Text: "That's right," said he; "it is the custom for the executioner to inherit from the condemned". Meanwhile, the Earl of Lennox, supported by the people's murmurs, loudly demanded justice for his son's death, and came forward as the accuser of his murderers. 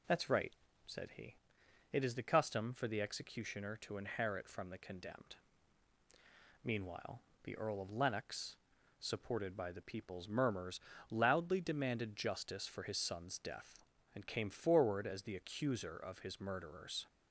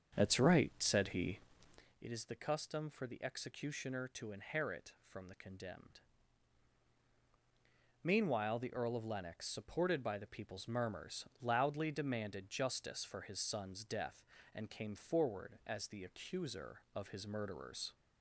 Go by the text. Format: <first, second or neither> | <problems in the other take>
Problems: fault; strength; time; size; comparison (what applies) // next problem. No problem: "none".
first | starts louder than the rest; strong; until 2.0 s; 7 dB